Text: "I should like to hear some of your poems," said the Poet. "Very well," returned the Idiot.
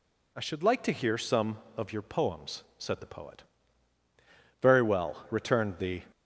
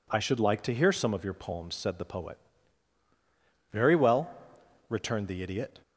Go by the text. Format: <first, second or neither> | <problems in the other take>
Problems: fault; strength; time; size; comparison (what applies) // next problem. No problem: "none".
second | stops before "Idiot"; at 6.1 s